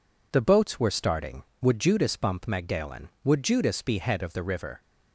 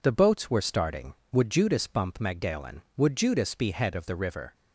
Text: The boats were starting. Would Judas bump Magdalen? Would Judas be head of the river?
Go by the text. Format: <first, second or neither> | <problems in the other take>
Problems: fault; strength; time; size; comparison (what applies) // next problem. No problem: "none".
neither | none